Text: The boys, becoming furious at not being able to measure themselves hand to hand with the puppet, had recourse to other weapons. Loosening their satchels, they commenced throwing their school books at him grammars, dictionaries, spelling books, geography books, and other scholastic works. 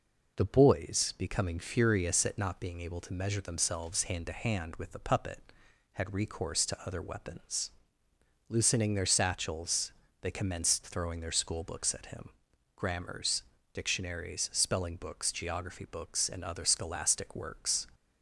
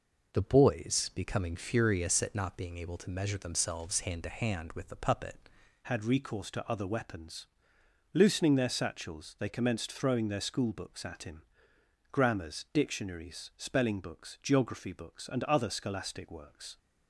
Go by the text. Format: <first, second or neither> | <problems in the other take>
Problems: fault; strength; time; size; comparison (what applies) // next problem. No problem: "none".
first | changes voice at "had"; from 5.8 s on; 10.9 s long // pauses between "him" and "grammars"; noticeable; at 11.4 s; 0.70 s long; noticeable in the first